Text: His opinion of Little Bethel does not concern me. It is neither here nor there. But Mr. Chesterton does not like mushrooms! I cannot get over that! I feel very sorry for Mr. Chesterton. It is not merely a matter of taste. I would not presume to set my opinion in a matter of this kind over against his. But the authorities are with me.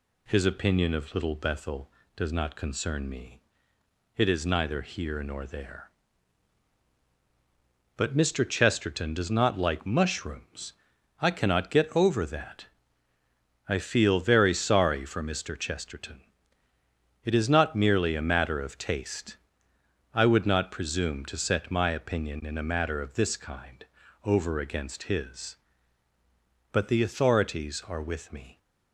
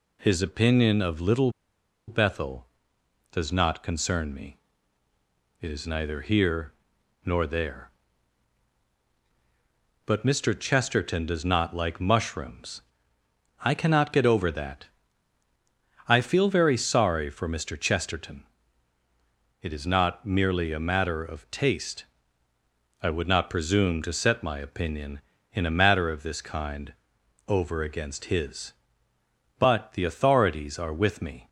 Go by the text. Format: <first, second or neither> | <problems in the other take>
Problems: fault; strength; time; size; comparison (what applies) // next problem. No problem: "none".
first | pauses between "Little" and "Bethel"; noticeable; at 1.4 s; 0.57 s long // pauses between "here" and "nor"; noticeable; at 6.7 s; 0.50 s long // pauses between "kind" and "over"; noticeable; at 26.9 s; 0.56 s long; also in the first